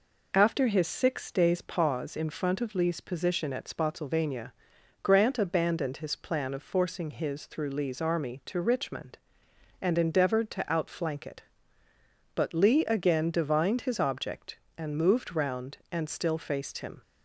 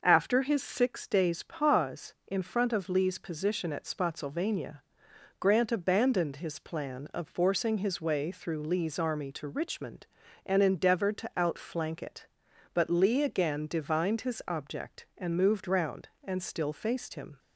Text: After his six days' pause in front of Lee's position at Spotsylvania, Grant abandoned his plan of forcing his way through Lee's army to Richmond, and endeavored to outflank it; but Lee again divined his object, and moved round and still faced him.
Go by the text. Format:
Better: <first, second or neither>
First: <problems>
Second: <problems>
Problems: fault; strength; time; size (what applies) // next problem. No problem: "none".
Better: second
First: skips "way"; at 7.4 s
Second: none